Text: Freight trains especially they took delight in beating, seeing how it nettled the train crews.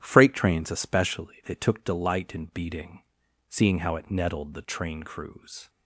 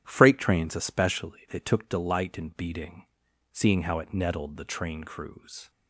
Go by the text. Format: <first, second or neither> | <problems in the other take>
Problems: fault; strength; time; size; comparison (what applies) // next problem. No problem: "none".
neither | starts louder than the rest; strong; the same in both